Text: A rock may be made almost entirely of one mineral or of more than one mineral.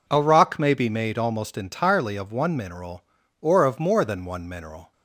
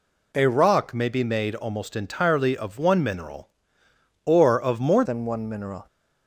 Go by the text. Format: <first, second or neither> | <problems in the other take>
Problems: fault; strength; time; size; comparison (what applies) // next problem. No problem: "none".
first | changes voice at "than"; from 5.0 s on; 0.8 s long